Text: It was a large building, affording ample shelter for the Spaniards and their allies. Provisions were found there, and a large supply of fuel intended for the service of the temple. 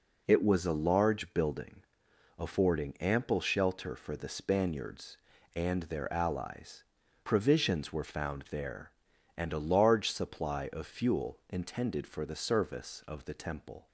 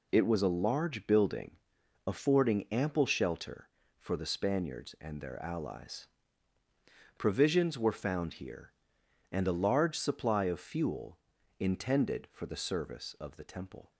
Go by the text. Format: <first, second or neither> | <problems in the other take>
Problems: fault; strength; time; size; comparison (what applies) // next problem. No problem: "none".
first | says "here" for "there"; at 8.3 s // pauses between "fuel" and "intended"; at 11.1 s; 0.40 s long